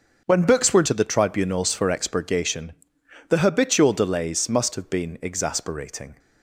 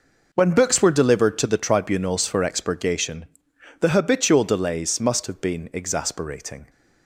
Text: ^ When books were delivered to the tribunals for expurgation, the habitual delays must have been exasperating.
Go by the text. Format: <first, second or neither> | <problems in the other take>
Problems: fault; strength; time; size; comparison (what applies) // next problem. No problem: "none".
second | starts louder than the rest; until 1.2 s; 7 dB // skips "delivered"; at 0.8 s